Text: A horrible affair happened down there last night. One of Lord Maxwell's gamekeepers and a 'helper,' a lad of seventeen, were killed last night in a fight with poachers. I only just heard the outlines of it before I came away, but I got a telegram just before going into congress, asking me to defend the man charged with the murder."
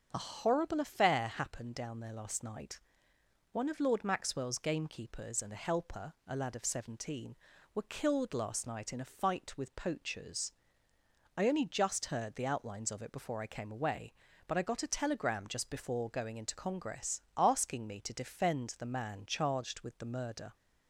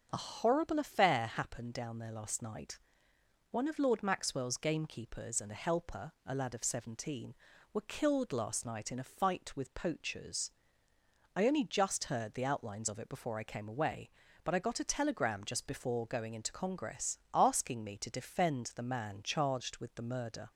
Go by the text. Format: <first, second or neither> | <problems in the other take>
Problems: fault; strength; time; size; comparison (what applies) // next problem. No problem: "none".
neither | starts louder than the rest; the same in both